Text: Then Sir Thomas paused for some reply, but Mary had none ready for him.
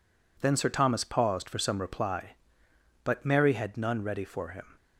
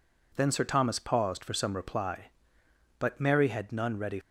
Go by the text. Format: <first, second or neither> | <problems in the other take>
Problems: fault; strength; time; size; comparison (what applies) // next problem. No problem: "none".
first | stops before "for him"; at 4.2 s